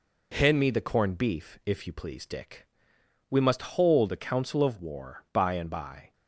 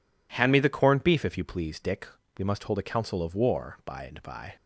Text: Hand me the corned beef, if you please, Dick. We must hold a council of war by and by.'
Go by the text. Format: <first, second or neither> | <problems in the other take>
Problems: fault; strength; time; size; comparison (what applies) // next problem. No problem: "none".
neither | none